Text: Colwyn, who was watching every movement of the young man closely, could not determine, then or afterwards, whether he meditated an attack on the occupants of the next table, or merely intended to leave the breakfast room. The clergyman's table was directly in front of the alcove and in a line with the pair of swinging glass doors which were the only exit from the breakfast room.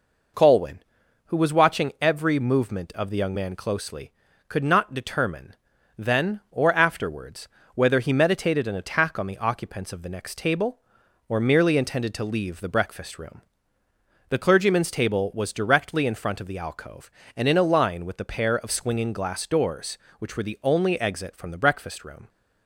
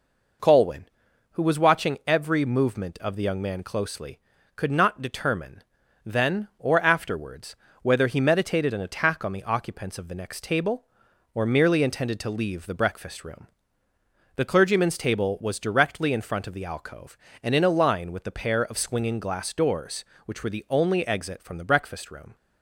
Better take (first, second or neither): neither